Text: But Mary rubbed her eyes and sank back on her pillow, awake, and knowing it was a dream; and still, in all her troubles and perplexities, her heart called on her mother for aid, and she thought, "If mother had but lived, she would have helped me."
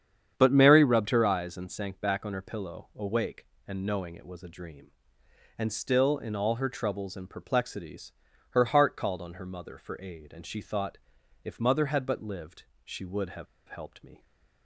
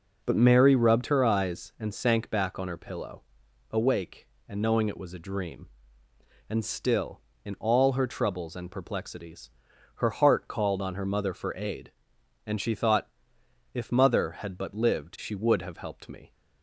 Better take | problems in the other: second | starts louder than the rest; strong; until 1.3 s; 8.5 dB // pauses between "have" and "helped"; slight; at 13.4 s; 0.22 s long

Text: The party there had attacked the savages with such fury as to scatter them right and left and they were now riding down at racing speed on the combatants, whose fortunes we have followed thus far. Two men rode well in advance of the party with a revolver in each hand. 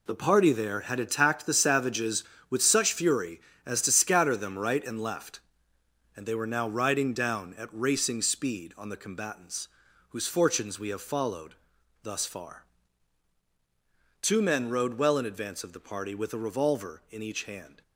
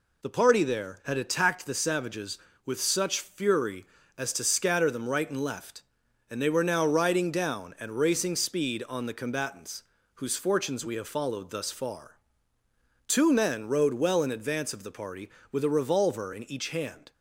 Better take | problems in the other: second | gets quieter; strong; throughout; 10 dB // pauses between "followed" and "thus"; noticeable; at 11.5 s; 0.48 s long

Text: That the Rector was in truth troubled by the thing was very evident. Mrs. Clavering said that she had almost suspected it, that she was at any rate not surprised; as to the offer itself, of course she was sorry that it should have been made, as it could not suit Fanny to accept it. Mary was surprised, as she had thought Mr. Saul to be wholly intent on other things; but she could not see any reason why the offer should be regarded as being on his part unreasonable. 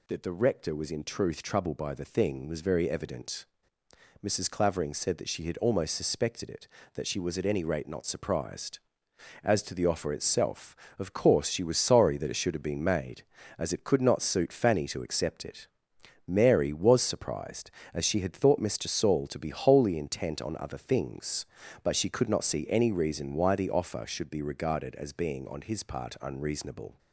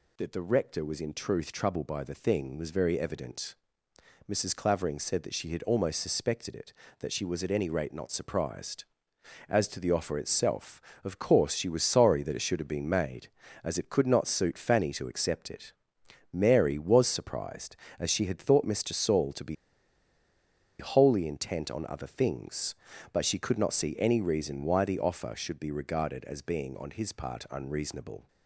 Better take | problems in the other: first | pauses between "be" and "wholly"; at 19.5 s; 1.2 s long

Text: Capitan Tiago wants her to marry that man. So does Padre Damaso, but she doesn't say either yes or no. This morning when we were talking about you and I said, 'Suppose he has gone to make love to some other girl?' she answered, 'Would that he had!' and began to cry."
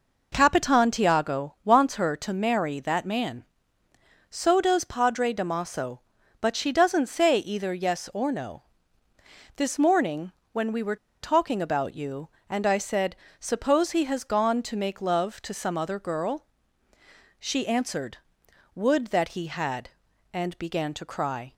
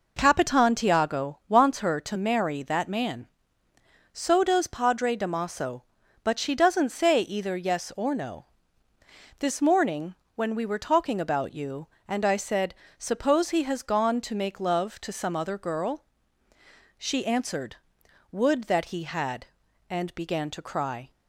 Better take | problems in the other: second | pauses between "morning" and "when"; slight; at 10.3 s; 0.20 s long; slight in the second // pauses between "were" and "talking"; slight; at 10.9 s; 0.27 s long

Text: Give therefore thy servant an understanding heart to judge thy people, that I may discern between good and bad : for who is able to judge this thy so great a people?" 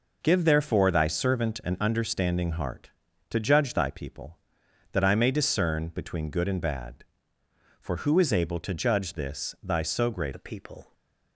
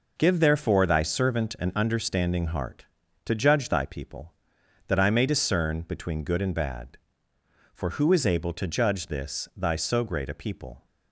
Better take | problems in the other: second | changes voice at "a"; from 10.3 s on; 0.6 s long

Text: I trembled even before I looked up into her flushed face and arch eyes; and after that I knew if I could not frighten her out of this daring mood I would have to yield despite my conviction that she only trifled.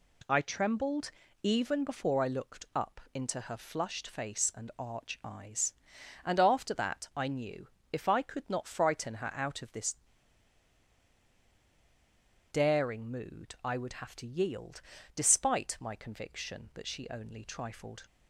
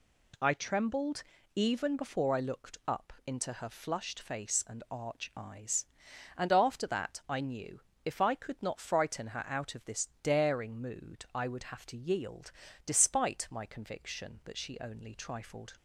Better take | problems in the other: second | pauses between "trembled" and "even"; slight; at 1.1 s; 0.32 s long; slight in the second // pauses between "knew" and "if"; slight; at 7.6 s; 0.24 s long; slight in the second // pauses between "this" and "daring"; strong; at 9.9 s; 2.5 s long // pauses between "yield" and "despite"; slight; at 14.8 s; 0.34 s long; slight in the second

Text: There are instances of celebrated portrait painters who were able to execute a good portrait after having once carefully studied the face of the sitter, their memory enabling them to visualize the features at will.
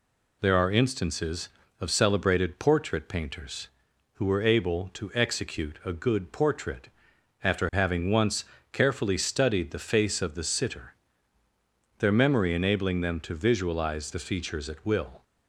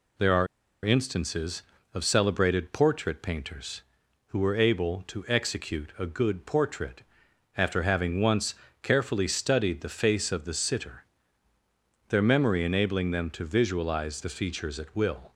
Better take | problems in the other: first | pauses between "are" and "instances"; at 0.4 s; 0.38 s long // pauses between "portrait" and "after"; noticeable; at 7.0 s; 0.54 s long; noticeable in the first // pauses between "once" and "carefully"; slight; at 8.5 s; 0.28 s long; slight in the first

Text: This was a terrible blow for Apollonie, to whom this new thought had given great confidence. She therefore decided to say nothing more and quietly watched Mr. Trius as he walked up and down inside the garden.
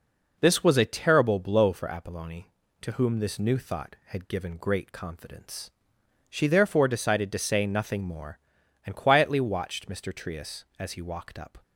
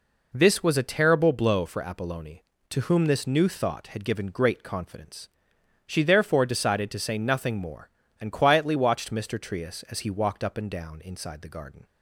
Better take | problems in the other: second | stops before "and down inside the garden"; at 11.6 s

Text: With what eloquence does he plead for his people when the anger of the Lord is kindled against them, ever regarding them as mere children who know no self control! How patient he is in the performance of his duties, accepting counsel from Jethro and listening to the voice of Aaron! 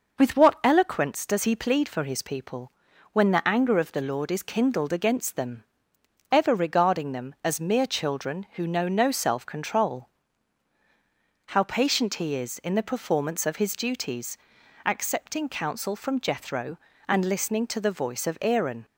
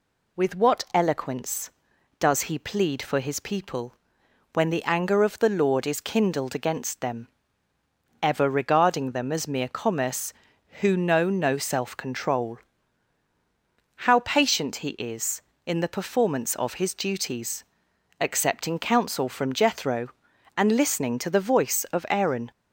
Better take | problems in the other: first | pauses between "people" and "when"; noticeable; at 3.9 s; 0.60 s long; also in the first // says "commerce" for "children"; at 9.6 s

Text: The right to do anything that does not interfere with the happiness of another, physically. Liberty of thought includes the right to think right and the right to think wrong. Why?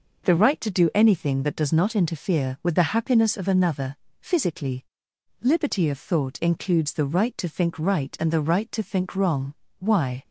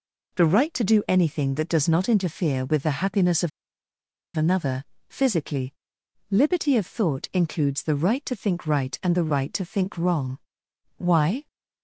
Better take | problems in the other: first | pauses between "of" and "another"; noticeable; at 3.4 s; 0.86 s long

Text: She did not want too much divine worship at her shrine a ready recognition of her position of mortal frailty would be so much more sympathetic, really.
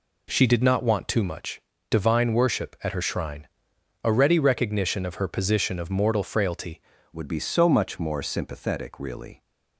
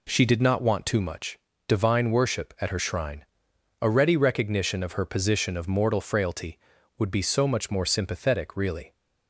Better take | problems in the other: second | pauses between "much" and "divine"; slight; at 1.5 s; 0.30 s long; slight in the second // pauses between "shrine" and "a"; noticeable; at 3.4 s; 0.56 s long; noticeable in the second // changes voice at "would"; from 7.1 s on; 2.3 s long

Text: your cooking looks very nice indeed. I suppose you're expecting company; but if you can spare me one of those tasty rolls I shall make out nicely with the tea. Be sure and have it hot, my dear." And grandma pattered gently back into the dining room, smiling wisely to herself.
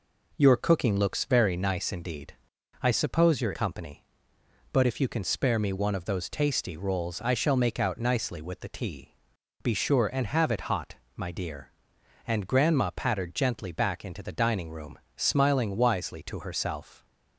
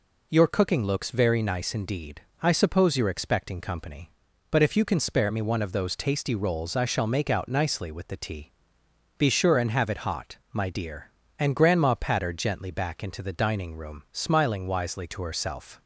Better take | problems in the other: second | skips "expecting"; at 3.5 s

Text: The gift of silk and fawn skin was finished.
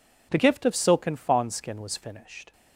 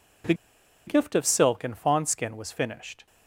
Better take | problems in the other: first | pauses between "The" and "gift"; noticeable; at 0.3 s; 0.53 s long

